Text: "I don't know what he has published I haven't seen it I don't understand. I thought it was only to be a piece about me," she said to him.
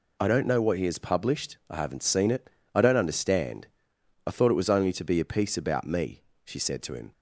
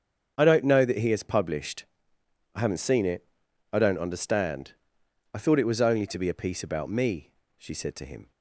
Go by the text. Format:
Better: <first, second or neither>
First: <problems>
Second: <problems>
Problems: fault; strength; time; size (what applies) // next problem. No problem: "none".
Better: first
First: pauses between "it" and "I"; slight; at 2.4 s; 0.24 s long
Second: starts louder than the rest; strong; until 1.4 s; 7.5 dB // says "that" for "what"; at 0.8 s // pauses between "published" and "I"; noticeable; at 1.8 s; 0.72 s long // pauses between "it" and "I"; noticeable; at 3.2 s; 0.48 s long